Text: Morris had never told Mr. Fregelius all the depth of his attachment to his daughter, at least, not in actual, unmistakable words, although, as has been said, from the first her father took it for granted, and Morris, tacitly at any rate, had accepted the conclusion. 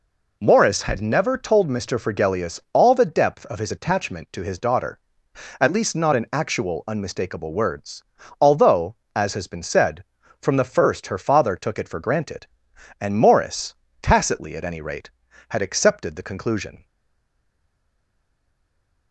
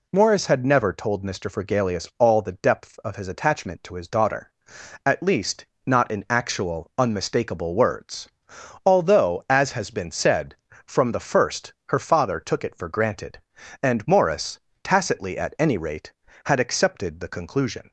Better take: second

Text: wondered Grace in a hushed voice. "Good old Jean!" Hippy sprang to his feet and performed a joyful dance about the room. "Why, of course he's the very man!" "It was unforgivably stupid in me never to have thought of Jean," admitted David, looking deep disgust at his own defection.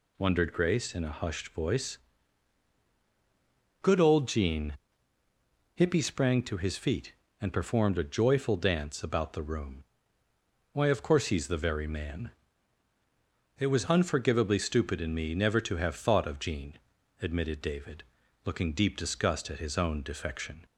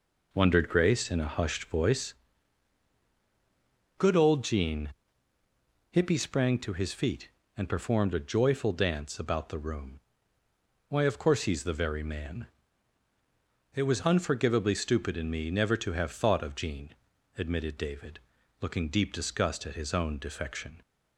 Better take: first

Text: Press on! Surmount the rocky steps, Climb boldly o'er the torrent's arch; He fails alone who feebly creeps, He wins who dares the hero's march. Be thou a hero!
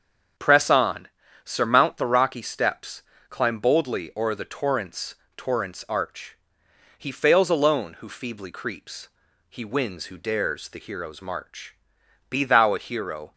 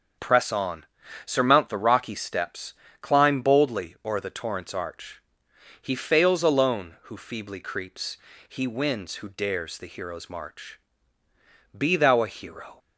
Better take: second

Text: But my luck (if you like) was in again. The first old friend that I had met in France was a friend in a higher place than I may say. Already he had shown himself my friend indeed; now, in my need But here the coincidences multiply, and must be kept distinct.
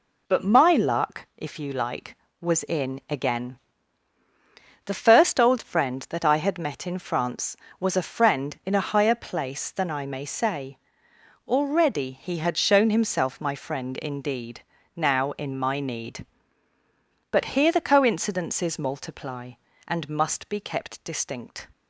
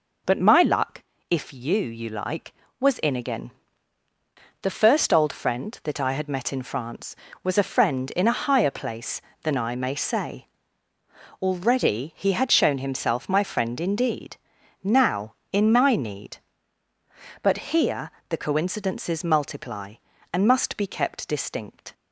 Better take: first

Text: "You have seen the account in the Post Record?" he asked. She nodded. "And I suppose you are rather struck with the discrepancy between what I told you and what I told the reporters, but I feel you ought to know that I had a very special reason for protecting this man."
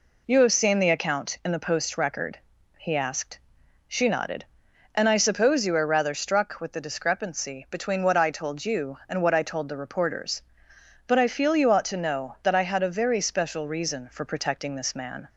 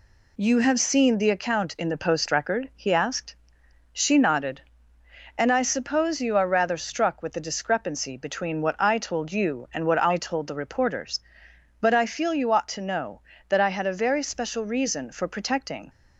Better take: first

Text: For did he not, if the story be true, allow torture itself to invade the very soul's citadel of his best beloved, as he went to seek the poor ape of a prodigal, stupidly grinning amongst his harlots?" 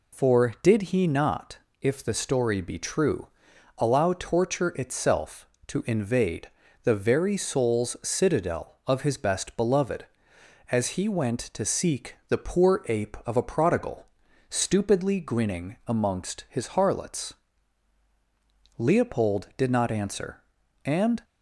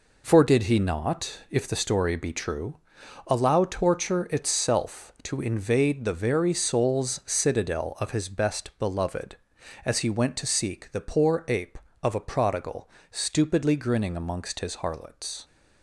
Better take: second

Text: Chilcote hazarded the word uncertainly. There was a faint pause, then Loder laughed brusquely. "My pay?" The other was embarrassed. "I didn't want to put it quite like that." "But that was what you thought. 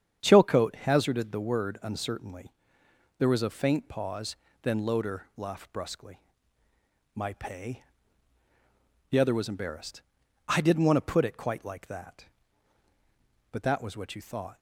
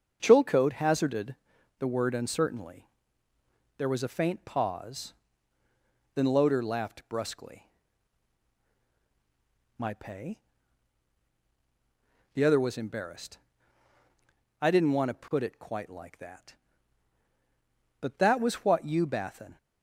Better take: first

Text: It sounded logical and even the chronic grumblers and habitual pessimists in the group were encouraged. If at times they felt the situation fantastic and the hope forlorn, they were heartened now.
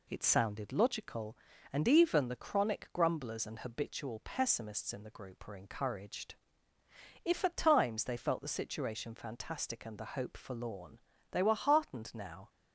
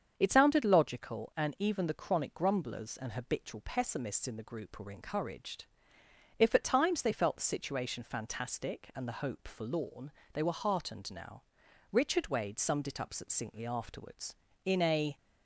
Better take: first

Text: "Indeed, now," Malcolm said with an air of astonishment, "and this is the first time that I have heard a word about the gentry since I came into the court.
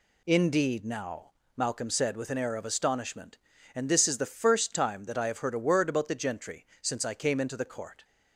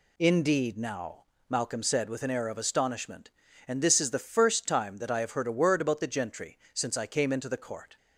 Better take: neither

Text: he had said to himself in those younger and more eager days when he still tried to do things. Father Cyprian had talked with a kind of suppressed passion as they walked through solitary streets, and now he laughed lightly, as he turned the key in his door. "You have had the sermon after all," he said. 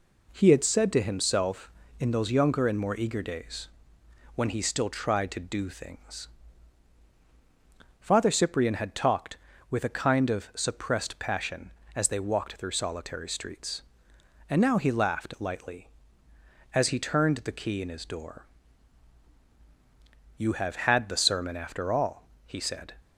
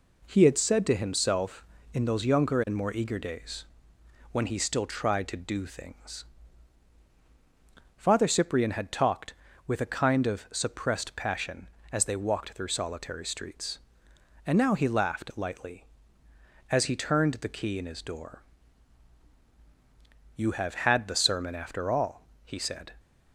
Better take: neither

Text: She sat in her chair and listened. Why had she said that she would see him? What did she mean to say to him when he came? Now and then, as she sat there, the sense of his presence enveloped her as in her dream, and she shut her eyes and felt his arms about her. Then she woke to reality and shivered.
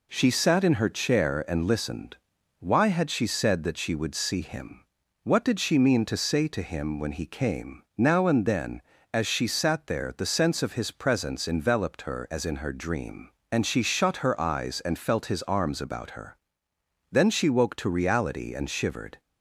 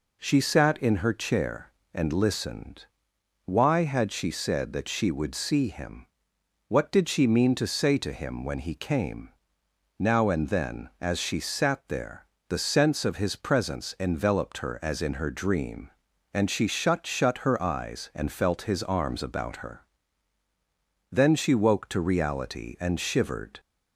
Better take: first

